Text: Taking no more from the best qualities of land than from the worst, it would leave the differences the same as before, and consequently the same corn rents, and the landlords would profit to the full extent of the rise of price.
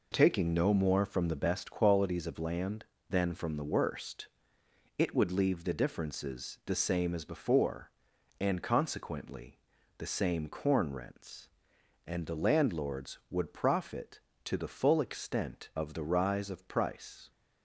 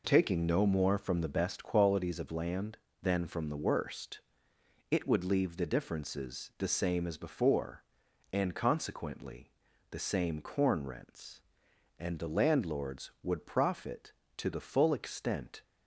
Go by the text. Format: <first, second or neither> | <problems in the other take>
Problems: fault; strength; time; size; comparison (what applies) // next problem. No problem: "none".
first | pauses between "consequently" and "the"; at 9.4 s; 0.40 s long; also in the first // stops before "of the rise of price"; at 15.6 s